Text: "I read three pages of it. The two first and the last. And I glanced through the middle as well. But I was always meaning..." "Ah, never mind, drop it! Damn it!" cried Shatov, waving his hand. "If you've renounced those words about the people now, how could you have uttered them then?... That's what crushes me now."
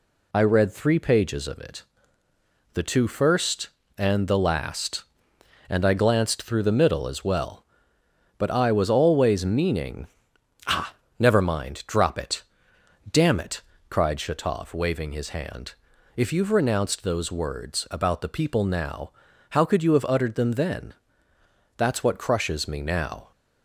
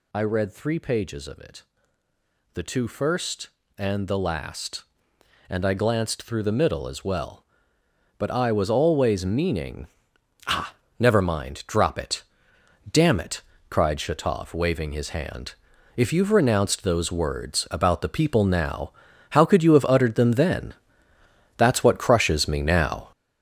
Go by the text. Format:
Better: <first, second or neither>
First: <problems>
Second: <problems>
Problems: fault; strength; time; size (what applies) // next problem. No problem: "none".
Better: first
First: none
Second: gets louder; throughout; 7 dB